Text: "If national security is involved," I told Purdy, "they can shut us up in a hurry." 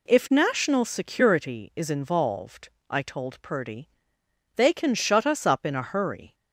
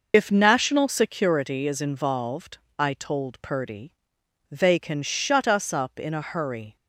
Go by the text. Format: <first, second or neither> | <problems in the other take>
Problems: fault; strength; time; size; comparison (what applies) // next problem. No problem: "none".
first | loses the start of "If"; at 0.1 s; 70 ms